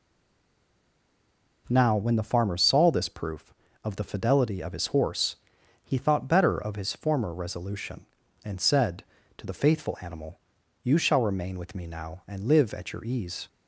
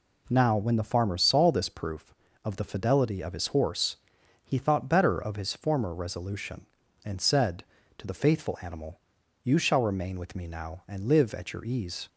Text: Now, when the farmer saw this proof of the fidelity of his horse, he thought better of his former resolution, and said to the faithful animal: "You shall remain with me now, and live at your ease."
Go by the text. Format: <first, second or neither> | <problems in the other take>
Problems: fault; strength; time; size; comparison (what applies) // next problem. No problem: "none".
second | stays silent before the first word; noticeable; until 1.6 s; 1.6 s long